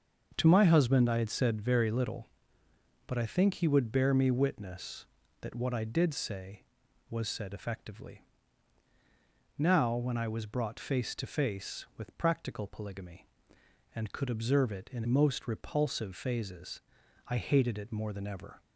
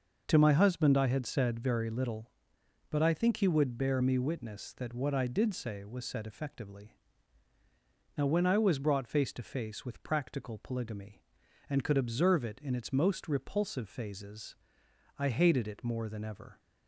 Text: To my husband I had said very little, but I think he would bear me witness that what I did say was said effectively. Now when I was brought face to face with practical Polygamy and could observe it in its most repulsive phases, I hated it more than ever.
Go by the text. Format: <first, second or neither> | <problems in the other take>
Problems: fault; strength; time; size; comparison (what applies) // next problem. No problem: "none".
second | starts louder than the rest; until 1.3 s; 6.5 dB // skips "its"; at 15.0 s